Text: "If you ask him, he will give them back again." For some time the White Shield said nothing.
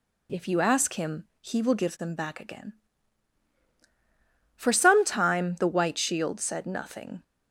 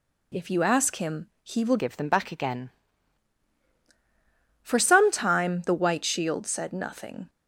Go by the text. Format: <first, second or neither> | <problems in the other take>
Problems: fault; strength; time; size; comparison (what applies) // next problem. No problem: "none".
first | changes voice from "give" to "again"; from 1.7 to 2.7 s; 1.0 s long